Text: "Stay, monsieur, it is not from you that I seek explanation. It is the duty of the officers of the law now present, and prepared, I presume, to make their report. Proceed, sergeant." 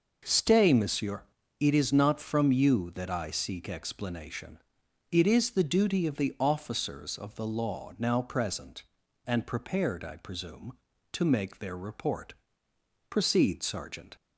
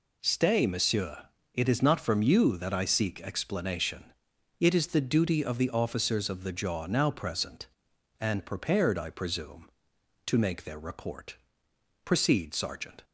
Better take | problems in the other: first | says "jaw" for "law"; at 6.5 s

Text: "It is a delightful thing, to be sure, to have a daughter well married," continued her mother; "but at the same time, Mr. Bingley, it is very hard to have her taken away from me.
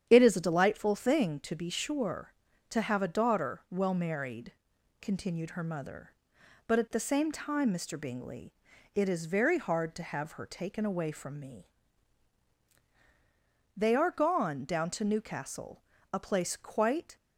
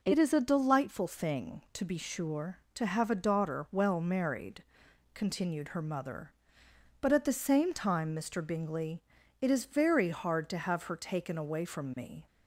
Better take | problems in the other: second | starts louder than the rest; strong; until 1.1 s; 9 dB // goes on to say "They are gone down to Newcastle a place quite"; strong; from 13.7 s on; 3.4 s long

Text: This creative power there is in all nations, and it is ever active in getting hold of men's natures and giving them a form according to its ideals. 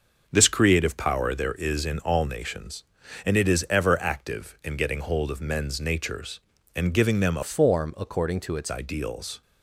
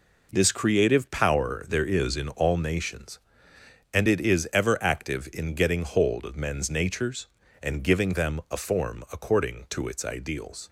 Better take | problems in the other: second | starts louder than the rest; until 1.2 s; 6 dB // changes voice from "form" to "its"; from 7.4 to 8.7 s; 1.3 s long

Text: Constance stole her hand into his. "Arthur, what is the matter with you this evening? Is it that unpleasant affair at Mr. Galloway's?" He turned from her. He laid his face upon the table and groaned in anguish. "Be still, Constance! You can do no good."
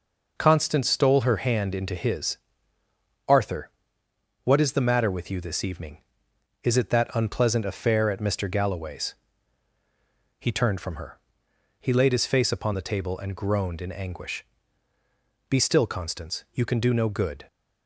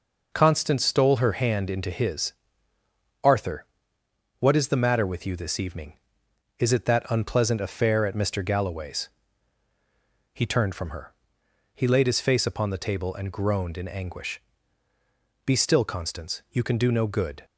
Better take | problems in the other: neither | none

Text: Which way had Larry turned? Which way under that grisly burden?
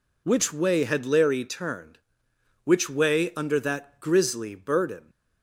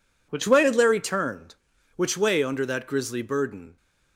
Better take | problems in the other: neither | none

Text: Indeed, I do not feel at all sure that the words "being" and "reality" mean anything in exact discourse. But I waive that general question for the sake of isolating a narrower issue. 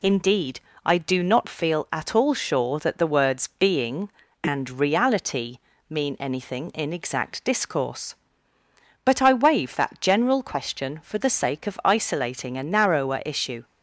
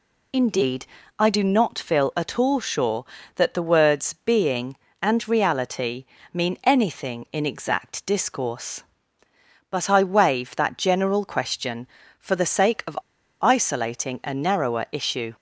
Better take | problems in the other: first | pauses between "reality" and "mean"; slight; at 6.0 s; 0.30 s long; slight in the first // pauses between "of" and "isolating"; at 12.9 s; 0.41 s long

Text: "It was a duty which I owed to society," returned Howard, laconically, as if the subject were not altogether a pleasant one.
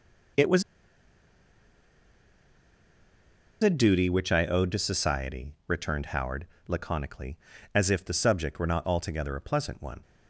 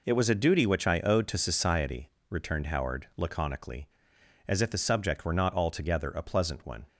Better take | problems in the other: second | pauses between "was" and "a"; strong; at 0.6 s; 3.0 s long

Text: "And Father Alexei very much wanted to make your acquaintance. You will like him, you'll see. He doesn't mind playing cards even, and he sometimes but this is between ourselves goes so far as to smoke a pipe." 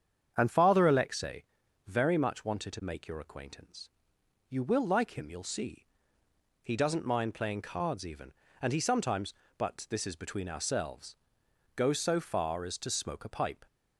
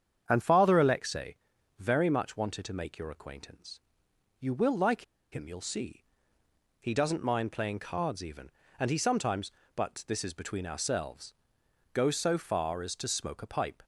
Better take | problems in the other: first | starts louder than the rest; strong; until 1.2 s; 8 dB; strong in the first // pauses between "Alexei" and "very"; at 1.3 s; 0.42 s long; also in the first // pauses between "like" and "him"; slight; at 5.0 s; 0.29 s long // pauses between "ourselves" and "goes"; noticeable; at 11.3 s; 0.62 s long; noticeable in the first

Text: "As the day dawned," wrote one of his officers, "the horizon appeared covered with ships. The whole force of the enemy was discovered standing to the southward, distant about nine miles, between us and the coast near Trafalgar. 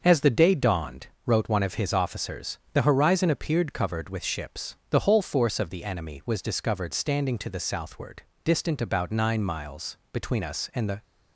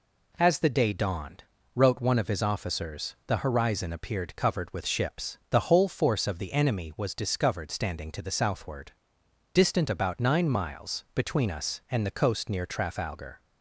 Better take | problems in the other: second | starts louder than the rest; until 1.0 s; 6.5 dB // stops before "coast near Trafalgar"; at 11.0 s

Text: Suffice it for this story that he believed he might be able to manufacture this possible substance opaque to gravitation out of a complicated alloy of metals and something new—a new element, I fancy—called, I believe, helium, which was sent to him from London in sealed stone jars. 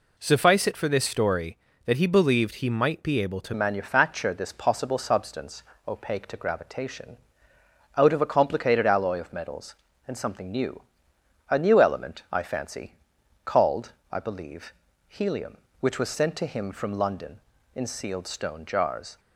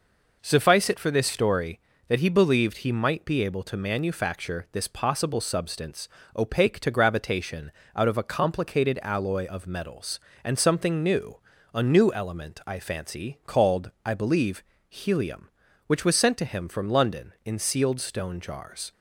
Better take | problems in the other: second | changes voice at "manufacture"; from 3.5 s on; 15.6 s long // pauses between "substance" and "opaque"; slight; at 5.6 s; 0.26 s long; slight in the second // pauses between "gravitation" and "out"; noticeable; at 7.1 s; 0.80 s long; slight in the second

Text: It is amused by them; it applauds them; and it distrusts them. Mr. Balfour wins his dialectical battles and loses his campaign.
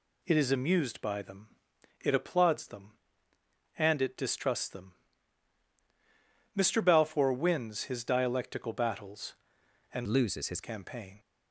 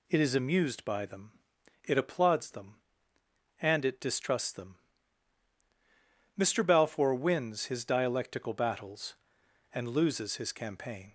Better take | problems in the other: second | changes voice from "loses" to "his"; from 10.0 to 10.6 s; 0.6 s long

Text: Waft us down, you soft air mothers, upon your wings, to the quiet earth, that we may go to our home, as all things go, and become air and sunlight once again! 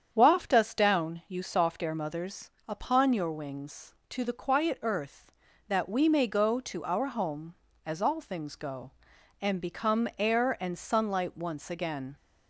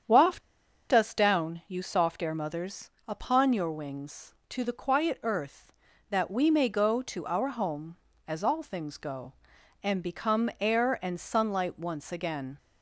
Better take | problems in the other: first | starts louder than the rest; strong; until 1.5 s; 8 dB; strong in the first // pauses between "Waft" and "us"; noticeable; at 0.4 s; 0.49 s long

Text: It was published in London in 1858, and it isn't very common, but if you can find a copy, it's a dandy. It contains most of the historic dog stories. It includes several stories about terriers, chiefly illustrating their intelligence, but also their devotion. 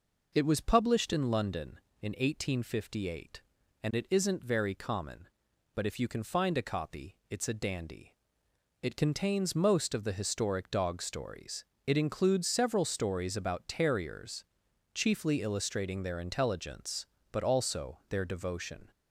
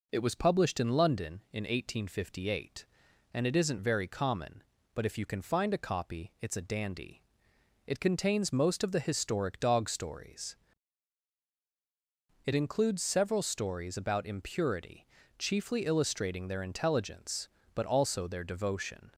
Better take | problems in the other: first | says "impurity" for "terriers"; at 14.2 s

